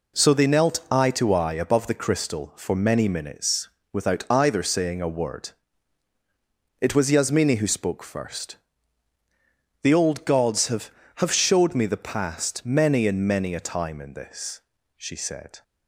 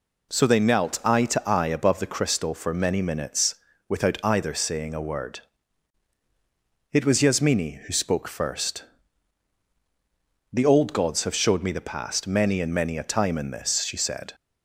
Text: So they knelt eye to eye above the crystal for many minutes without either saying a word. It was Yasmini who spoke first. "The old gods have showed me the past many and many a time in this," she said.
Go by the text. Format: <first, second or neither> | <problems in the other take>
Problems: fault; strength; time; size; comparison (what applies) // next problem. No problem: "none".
second | pauses between "minutes" and "without"; slight; at 3.6 s; 0.26 s long; slight in the second // says "have" twice; at 11.1 s